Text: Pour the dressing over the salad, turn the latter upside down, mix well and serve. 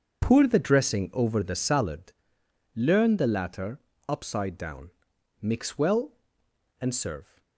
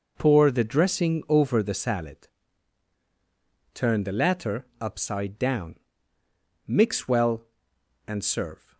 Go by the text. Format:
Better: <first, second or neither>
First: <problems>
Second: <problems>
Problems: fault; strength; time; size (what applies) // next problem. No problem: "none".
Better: second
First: starts louder than the rest; until 1.2 s; 7 dB // says "learn" for "turn"; at 2.7 s // pauses between "latter" and "upside"; slight; at 3.8 s; 0.26 s long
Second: none